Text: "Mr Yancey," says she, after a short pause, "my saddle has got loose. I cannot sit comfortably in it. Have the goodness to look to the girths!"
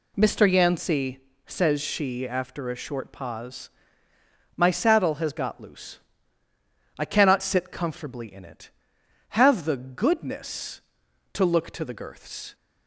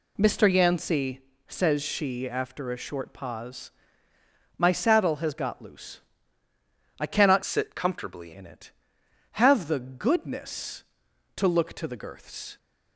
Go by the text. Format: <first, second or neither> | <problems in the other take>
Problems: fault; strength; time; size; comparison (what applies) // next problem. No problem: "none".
first | changes voice from "sit" to "comfortably"; from 7.4 to 8.3 s; 0.9 s long